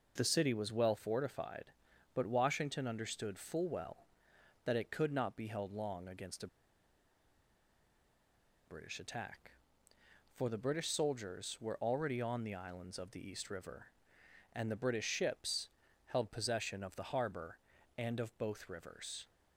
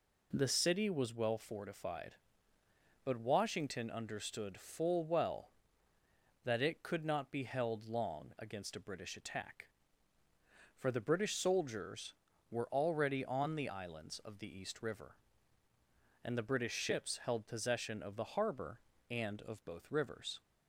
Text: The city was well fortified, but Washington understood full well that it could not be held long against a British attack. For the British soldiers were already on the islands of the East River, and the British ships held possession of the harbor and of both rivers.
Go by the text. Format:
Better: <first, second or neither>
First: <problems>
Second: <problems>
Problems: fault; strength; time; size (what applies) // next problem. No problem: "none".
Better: second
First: pauses between "a" and "British"; strong; at 6.4 s; 2.2 s long // pauses between "ships" and "held"; at 15.6 s; 0.38 s long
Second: none